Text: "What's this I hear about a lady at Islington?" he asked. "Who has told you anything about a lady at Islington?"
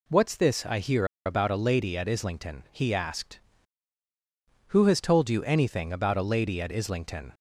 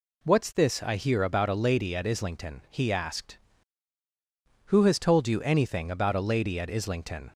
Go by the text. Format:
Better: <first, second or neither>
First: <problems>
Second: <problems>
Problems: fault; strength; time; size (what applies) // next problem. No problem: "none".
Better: second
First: pauses between "hear" and "about"; slight; at 1.0 s; 0.19 s long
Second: none